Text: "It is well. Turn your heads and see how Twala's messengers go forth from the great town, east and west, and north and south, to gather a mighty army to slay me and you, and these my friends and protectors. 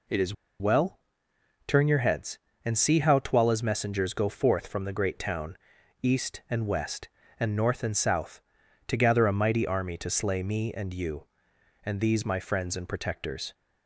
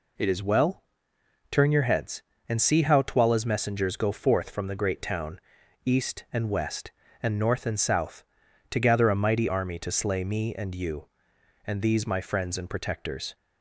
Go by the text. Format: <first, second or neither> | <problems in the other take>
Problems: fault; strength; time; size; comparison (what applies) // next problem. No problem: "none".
second | pauses between "is" and "well"; slight; at 0.3 s; 0.27 s long